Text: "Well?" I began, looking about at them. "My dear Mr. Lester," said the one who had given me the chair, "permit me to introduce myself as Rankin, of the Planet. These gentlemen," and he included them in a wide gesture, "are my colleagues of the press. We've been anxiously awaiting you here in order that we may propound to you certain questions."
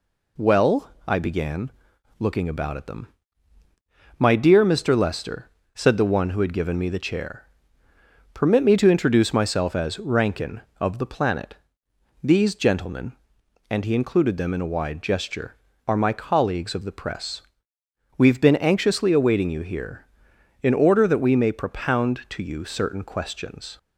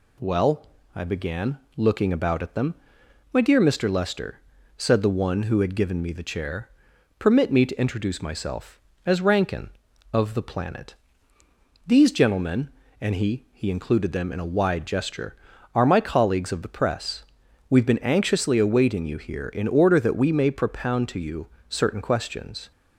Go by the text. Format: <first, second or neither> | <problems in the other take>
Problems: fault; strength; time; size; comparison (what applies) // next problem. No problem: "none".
first | says "he" twice; at 13.5 s // pauses between "you" and "certain"; slight; at 21.4 s; 0.22 s long